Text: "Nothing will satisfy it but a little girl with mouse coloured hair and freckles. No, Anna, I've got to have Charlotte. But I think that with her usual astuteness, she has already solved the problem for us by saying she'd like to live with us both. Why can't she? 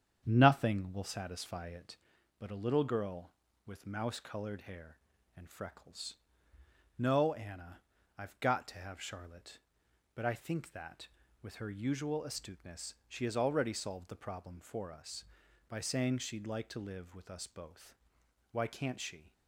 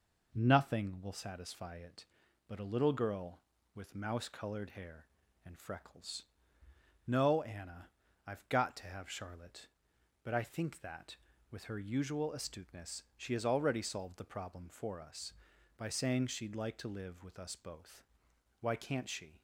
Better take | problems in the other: second | starts louder than the rest; strong; until 2.2 s; 8 dB

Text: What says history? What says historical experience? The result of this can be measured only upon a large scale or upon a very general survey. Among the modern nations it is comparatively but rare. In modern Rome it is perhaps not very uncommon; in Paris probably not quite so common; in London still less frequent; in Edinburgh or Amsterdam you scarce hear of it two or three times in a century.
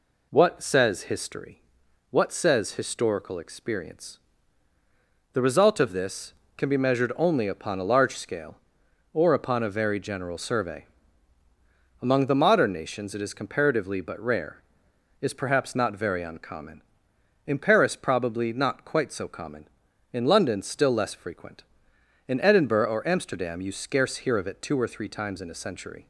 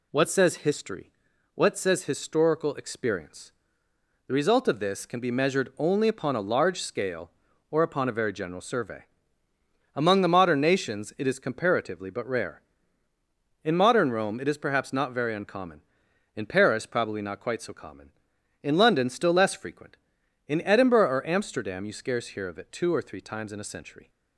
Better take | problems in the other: second | skips "In modern Rome it"; at 14.9 s

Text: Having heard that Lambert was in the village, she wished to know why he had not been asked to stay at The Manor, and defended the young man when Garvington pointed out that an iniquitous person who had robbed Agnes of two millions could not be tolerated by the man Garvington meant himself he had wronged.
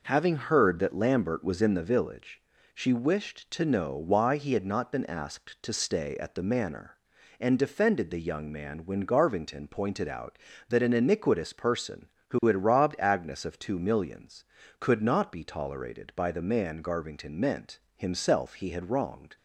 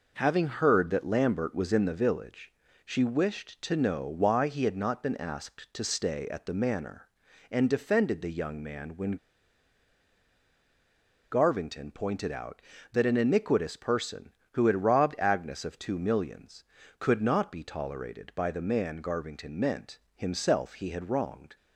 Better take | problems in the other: first | pauses between "when" and "Garvington"; strong; at 9.1 s; 2.1 s long // pauses between "meant" and "himself"; slight; at 19.9 s; 0.18 s long; slight in the first

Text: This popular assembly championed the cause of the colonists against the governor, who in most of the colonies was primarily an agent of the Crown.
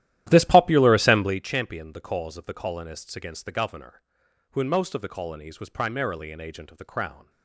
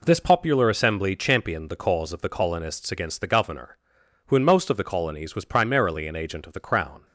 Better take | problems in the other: second | starts louder than the rest; strong; until 1.5 s; 13 dB

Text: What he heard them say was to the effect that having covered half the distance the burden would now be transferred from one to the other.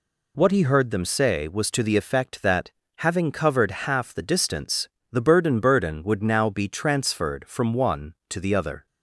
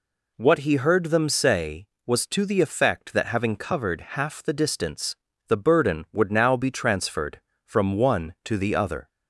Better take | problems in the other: second | pauses between "that" and "having"; slight; at 2.6 s; 0.26 s long // pauses between "distance" and "the"; slight; at 4.8 s; 0.24 s long; slight in the second // says "burden" twice; at 5.5 s

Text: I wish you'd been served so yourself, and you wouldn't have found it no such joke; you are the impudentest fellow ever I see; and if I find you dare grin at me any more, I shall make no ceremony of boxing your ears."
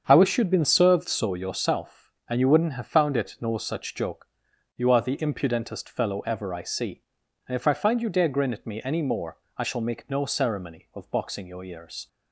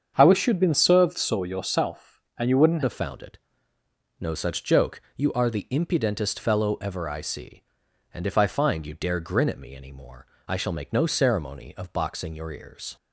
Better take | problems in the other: first | starts louder than the rest; strong; until 1.1 s; 7.5 dB; strong in the first // changes voice at "have"; from 2.8 s on; 10.1 s long // pauses between "it" and "no"; noticeable; at 3.3 s; 0.84 s long

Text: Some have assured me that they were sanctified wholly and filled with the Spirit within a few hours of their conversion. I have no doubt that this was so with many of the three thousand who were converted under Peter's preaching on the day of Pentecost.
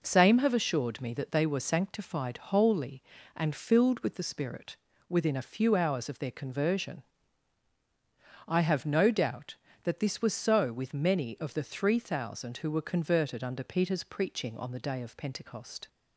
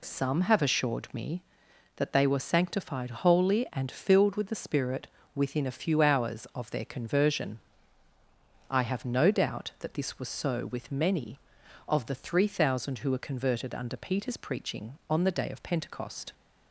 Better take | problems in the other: second | says "Same" for "Some"; at 0.0 s // pauses between "Spirit" and "within"; slight; at 4.7 s; 0.34 s long; slight in the second

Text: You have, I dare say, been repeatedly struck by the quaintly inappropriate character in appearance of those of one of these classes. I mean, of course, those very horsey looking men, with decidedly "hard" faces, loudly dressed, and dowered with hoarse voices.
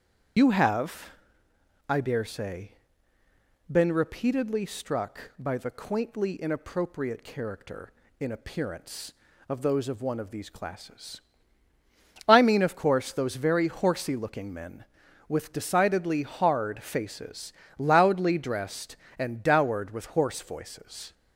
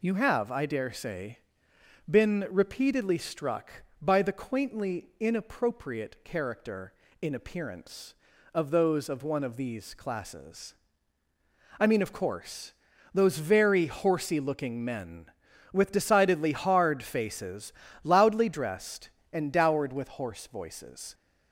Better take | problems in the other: second | loses the start of "You"; at 0.3 s; 90 ms // starts louder than the rest; strong; until 2.1 s; 8.5 dB

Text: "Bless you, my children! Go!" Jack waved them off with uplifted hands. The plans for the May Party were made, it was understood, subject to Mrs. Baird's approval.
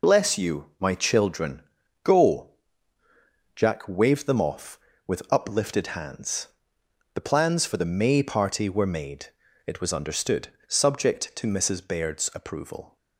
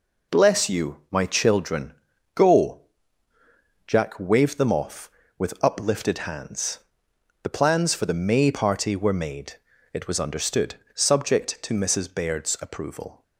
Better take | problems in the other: second | loses the start of "Bless"; at 0.0 s; 40 ms

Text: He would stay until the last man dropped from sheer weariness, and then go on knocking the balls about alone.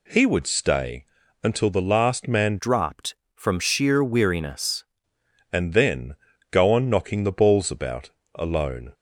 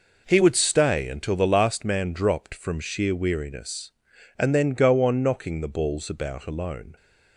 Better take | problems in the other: second | pauses between "stay" and "until"; at 1.0 s; 0.40 s long // changes voice from "dropped" to "weariness"; from 2.5 to 4.8 s; 2.3 s long // pauses between "then" and "go"; slight; at 6.1 s; 0.36 s long // pauses between "about" and "alone"; slight; at 8.0 s; 0.26 s long

